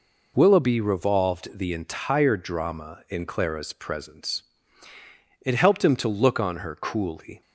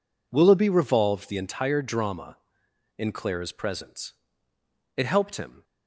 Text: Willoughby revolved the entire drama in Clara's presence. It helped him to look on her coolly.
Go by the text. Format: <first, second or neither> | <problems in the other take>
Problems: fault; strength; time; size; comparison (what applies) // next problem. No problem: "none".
first | stops before "to look on her coolly"; at 5.6 s